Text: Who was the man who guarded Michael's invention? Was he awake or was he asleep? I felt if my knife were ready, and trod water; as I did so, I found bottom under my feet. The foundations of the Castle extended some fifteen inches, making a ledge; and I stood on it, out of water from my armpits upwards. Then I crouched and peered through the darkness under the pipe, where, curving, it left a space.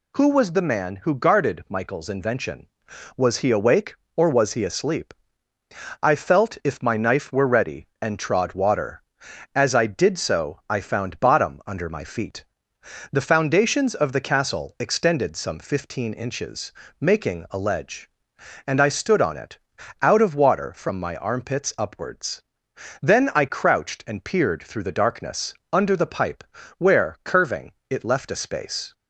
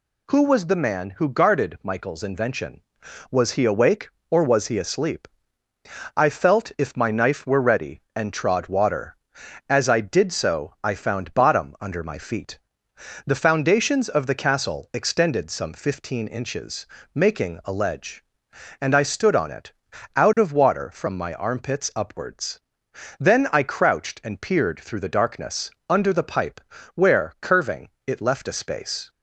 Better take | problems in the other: neither | pauses between "darkness" and "under"; slight; the same in both

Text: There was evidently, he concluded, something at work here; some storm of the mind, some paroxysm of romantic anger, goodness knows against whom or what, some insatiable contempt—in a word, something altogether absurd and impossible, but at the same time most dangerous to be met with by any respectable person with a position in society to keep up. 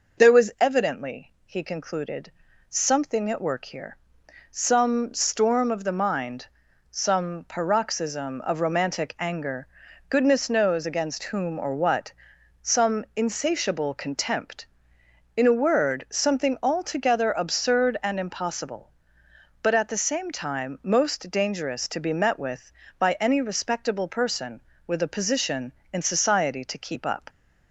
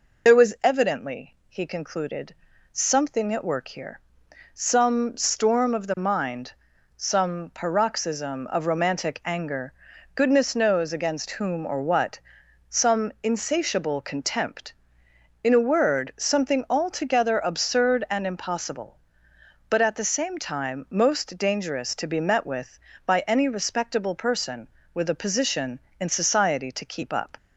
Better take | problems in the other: first | loses the start of "There"; at 0.2 s; 45 ms

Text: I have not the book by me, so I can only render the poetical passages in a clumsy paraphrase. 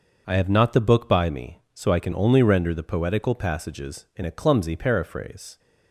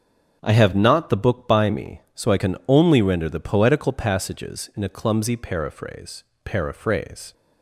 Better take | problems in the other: first | starts louder than the rest; strong; until 1.4 s; 7.5 dB; noticeable in the first // says "paraphrase" twice; at 6.4 s

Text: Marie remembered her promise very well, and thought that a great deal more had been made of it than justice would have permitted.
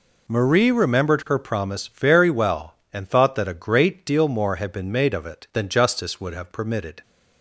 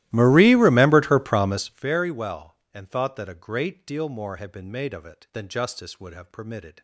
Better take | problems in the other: first | starts louder than the rest; strong; until 1.9 s; 16 dB

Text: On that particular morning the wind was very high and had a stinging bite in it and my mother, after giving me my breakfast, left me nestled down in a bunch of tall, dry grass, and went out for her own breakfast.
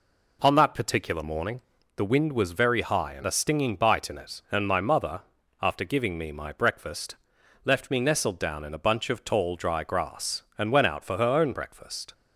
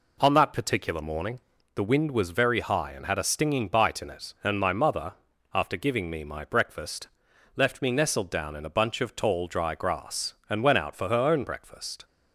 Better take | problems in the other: second | pauses between "morning" and "the"; slight; at 1.6 s; 0.36 s long; slight in the second // skips "had"; at 3.2 s

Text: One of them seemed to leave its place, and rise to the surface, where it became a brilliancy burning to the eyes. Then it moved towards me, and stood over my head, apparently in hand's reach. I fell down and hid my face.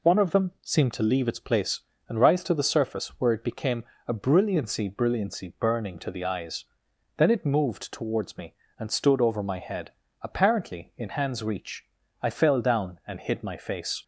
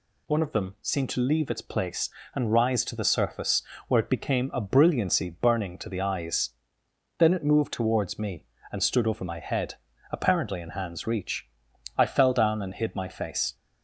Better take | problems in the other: second | pauses between "became" and "a"; slight; at 3.8 s; 0.22 s long // says "brilliancy" twice; at 4.8 s

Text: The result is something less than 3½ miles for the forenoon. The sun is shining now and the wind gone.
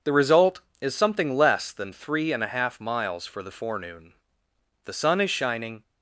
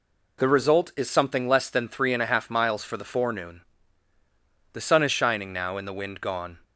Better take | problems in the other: second | stops before "now and the wind gone"; at 5.8 s

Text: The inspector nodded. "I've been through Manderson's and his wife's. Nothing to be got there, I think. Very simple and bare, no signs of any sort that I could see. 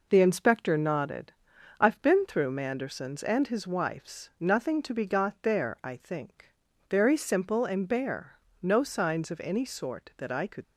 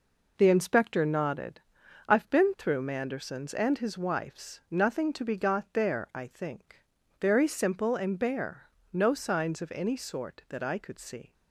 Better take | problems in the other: second | stops before "see"; at 10.6 s

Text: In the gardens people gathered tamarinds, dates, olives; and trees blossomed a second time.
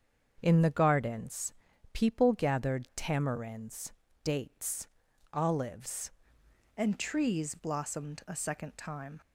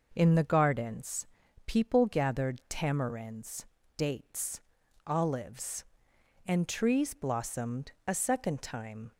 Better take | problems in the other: second | starts louder than the rest; until 1.4 s; 7 dB // pauses between "gardens" and "people"; at 1.5 s; 0.38 s long; also in the second // changes voice at "and"; from 6.7 s on; 2.5 s long

